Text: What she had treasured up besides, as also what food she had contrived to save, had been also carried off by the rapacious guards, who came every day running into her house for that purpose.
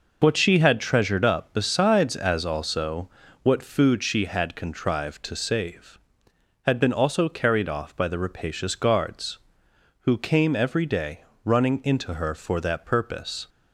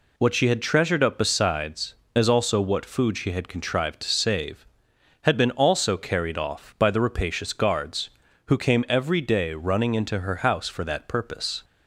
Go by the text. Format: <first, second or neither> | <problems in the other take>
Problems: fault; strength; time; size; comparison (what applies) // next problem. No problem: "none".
second | pauses between "also" and "what"; slight; at 3.0 s; 0.34 s long // pauses between "day" and "running"; slight; at 11.2 s; 0.18 s long // skips "house"; at 12.3 s